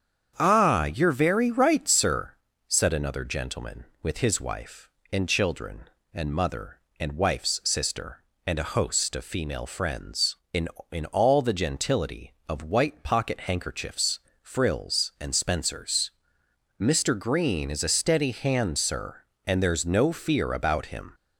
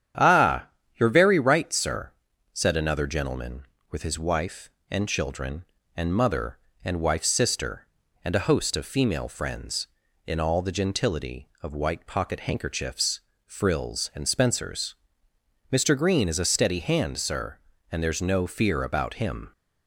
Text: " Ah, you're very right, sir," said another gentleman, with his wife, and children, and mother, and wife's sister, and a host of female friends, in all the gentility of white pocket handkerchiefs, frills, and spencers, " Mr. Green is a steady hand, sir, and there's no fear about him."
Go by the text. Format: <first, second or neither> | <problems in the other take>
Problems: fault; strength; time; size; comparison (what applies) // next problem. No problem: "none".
second | starts louder than the rest; strong; until 1.3 s; 8 dB; strong in the second // says "in" twice; at 10.9 s